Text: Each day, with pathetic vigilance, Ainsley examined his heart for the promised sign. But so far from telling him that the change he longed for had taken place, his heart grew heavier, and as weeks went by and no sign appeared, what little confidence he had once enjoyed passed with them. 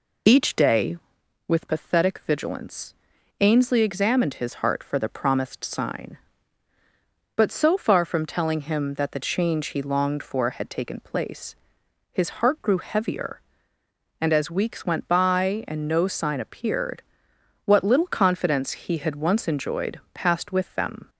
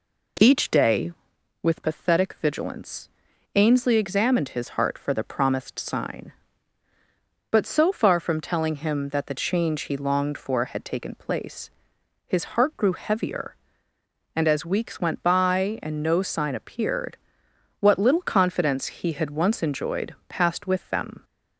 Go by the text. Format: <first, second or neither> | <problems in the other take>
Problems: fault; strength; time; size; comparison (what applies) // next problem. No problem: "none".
second | loses the start of "Each"; at 0.2 s; 35 ms